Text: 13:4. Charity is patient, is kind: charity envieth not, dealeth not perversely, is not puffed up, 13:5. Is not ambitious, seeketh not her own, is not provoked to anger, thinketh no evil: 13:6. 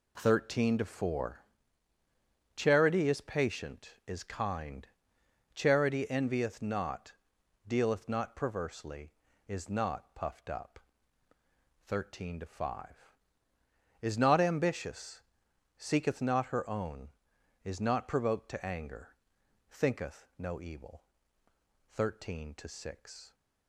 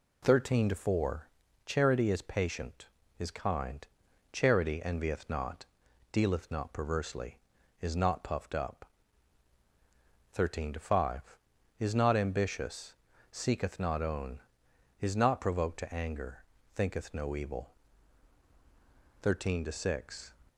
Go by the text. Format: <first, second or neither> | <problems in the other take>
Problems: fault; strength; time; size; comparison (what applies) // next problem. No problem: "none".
first | skips "her"; at 14.0 s